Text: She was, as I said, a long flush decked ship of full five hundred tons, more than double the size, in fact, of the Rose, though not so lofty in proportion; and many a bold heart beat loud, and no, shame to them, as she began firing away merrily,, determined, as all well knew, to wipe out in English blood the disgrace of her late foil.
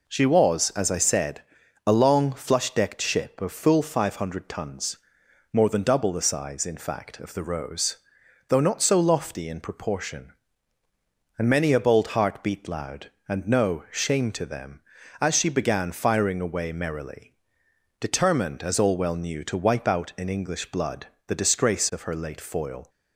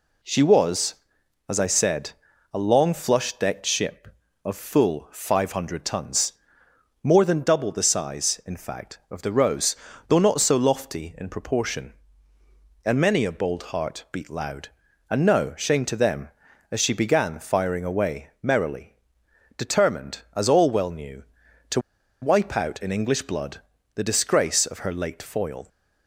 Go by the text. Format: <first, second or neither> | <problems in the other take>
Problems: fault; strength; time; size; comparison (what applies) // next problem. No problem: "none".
first | pauses between "to" and "wipe"; at 21.7 s; 0.42 s long // pauses between "blood" and "the"; slight; at 23.5 s; 0.36 s long; slight in the first